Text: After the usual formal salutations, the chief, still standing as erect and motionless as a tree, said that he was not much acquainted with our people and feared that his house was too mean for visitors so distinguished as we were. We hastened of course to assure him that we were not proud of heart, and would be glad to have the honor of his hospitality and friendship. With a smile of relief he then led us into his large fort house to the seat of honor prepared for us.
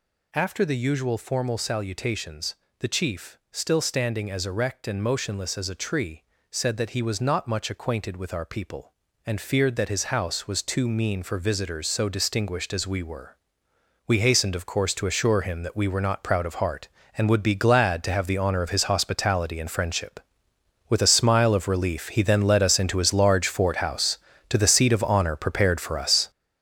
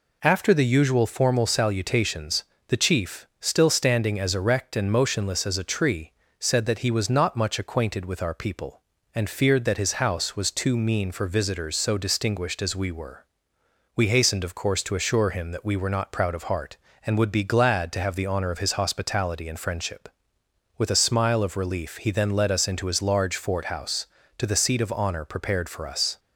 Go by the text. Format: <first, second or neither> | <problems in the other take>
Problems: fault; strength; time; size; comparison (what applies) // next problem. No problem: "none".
second | gets louder; strong; throughout; 8.5 dB